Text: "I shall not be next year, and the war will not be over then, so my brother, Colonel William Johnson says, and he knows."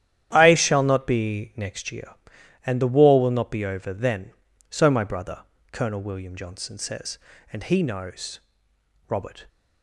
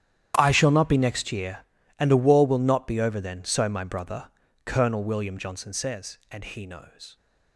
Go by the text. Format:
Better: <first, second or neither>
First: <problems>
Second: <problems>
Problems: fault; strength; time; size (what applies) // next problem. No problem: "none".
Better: second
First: starts louder than the rest; strong; until 1.3 s; 11 dB // goes on to say "Robert"; slight; from 9.0 s on; 0.36 s long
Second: starts louder than the rest; strong; until 1.3 s; 10 dB